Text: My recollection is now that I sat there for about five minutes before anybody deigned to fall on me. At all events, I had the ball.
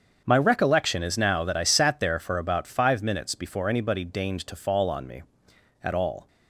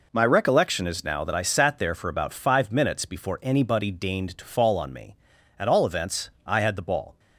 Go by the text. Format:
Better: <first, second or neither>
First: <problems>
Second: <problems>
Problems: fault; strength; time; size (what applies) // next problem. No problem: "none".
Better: second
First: starts louder than the rest; until 1.2 s; 7 dB // stops before "events I had the ball"; at 6.2 s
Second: none